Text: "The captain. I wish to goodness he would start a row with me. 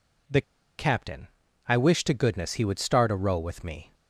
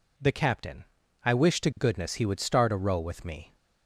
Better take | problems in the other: second | pauses between "The" and "captain"; at 0.4 s; 0.36 s long

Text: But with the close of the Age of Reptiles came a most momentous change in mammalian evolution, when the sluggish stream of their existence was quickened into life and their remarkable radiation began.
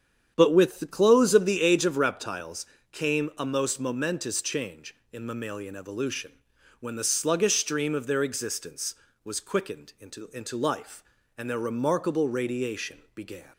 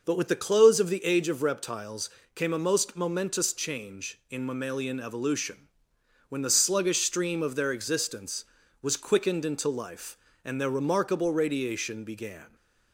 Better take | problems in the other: second | starts louder than the rest; strong; until 1.3 s; 8.5 dB // pauses between "Reptiles" and "came"; slight; at 2.6 s; 0.26 s long; slight in the second // says "into" twice; at 10.3 s // pauses between "radiation" and "began"; slight; at 12.9 s; 0.16 s long

